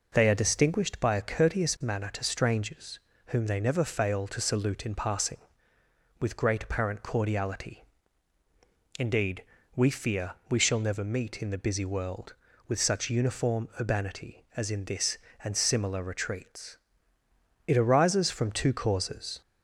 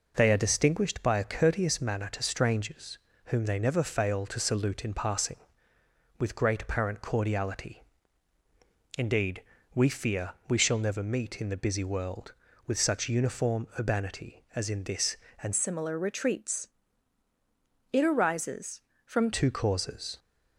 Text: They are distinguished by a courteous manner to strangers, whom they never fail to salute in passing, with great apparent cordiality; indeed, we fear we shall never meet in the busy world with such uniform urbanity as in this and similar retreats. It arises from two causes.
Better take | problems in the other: first | pauses between "fear" and "we"; slight; at 10.3 s; 0.16 s long; slight in the first // changes voice from "similar" to "from"; from 15.5 to 19.3 s; 3.8 s long

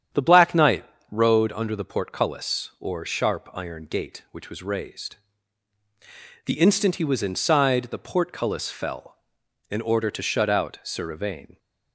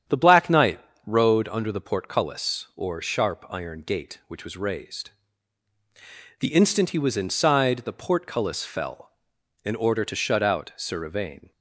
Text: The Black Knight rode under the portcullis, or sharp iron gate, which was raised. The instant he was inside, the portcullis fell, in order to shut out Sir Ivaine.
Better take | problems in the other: neither | starts louder than the rest; strong; the same in both // pauses between "Knight" and "rode"; slight; the same in both

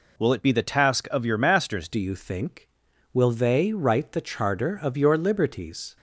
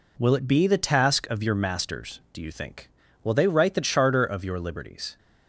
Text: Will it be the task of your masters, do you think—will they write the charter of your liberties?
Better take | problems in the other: second | changes voice at "do"; from 1.9 s on; 4.0 s long

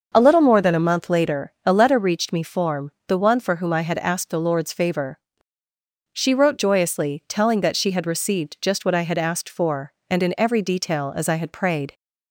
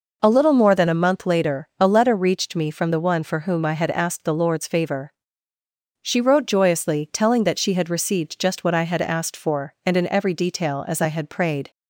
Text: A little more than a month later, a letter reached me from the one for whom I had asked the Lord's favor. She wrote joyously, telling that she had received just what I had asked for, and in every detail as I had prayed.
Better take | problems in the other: second | starts louder than the rest; until 1.1 s; 6 dB // says "form" for "from"; at 2.4 s

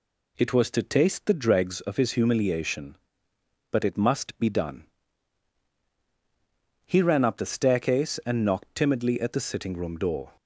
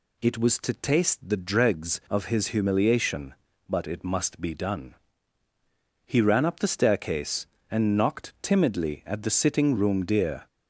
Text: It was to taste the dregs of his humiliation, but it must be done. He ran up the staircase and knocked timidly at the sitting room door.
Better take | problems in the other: first | says "deer" for "door"; at 10.0 s

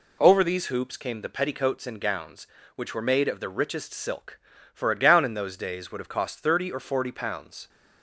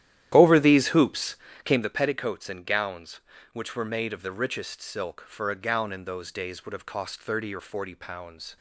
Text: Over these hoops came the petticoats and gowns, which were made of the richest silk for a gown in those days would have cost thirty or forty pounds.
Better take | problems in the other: first | starts louder than the rest; strong; until 1.8 s; 12 dB // pauses between "hoops" and "came"; slight; at 1.3 s; 0.28 s long

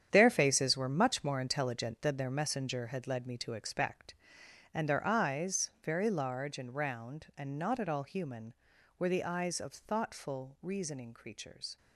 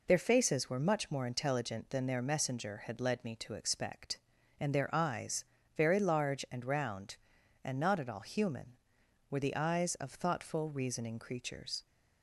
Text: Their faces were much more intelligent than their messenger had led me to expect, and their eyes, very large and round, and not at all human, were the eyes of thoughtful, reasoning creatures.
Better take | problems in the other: second | gets quieter; strong; throughout; 10.5 dB

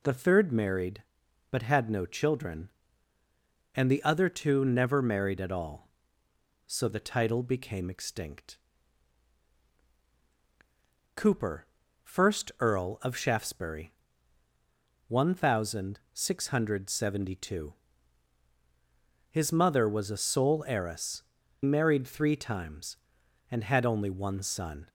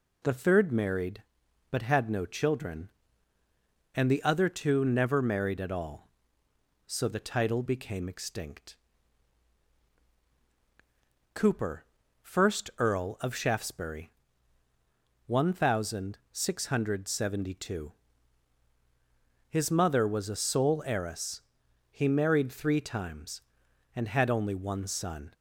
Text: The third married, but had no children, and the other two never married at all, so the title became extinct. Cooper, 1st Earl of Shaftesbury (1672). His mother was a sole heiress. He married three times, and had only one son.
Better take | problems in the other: second | skips "He"; at 21.4 s

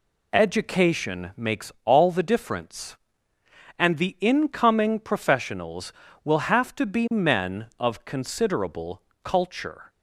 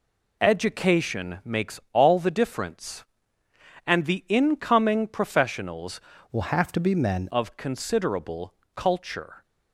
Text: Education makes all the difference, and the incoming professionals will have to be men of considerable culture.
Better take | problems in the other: first | changes voice from "will" to "men"; from 6.3 to 7.2 s; 0.9 s long // pauses between "considerable" and "culture"; slight; at 8.5 s; 0.20 s long; slight in the first

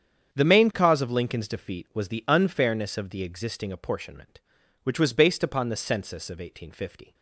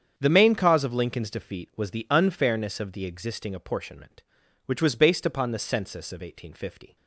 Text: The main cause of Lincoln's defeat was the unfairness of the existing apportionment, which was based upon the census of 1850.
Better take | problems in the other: neither | starts louder than the rest; strong; the same in both

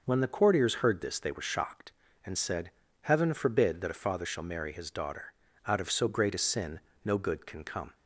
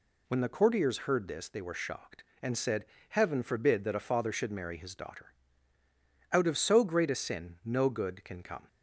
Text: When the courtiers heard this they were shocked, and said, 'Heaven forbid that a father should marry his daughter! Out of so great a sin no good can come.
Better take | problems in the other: second | says "shall" for "should"; at 4.2 s // pauses between "sin" and "no"; slight; at 6.7 s; 0.26 s long

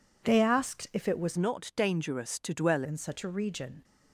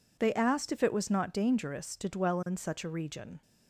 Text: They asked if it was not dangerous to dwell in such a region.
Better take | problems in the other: second | changes voice from "not" to "dwell"; from 1.3 to 2.8 s; 1.5 s long

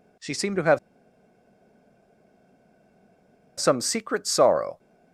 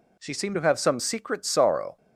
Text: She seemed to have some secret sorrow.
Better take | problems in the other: second | pauses between "have" and "some"; strong; at 0.7 s; 2.8 s long

